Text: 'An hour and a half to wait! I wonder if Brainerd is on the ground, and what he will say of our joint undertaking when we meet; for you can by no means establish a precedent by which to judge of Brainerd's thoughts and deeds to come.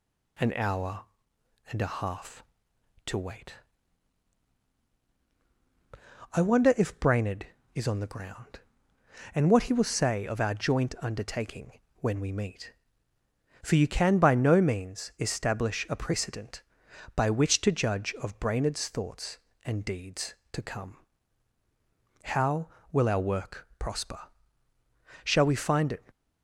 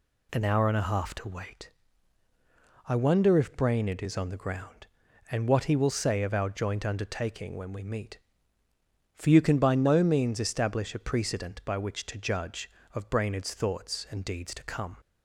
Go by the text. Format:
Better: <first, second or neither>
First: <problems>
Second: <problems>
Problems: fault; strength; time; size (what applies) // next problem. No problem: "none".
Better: second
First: pauses between "undertaking" and "when"; slight; at 11.7 s; 0.22 s long // goes on to say "How will our work prosper Shall we find it"; strong; from 22.2 s on; 3.8 s long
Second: none